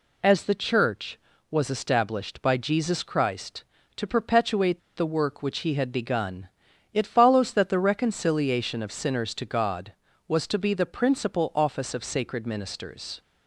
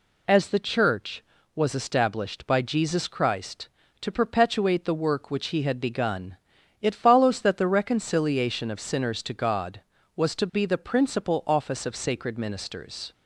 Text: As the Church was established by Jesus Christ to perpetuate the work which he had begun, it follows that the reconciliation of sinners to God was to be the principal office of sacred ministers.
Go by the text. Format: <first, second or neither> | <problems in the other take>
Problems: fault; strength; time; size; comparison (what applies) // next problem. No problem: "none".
second | pauses between "perpetuate" and "the"; slight; at 4.8 s; 0.16 s long